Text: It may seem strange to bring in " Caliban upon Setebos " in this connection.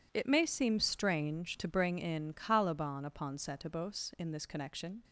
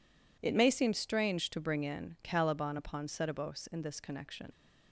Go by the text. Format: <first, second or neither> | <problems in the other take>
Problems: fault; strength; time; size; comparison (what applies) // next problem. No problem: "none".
first | leaves "connection" unfinished; at 4.5 s; 60 ms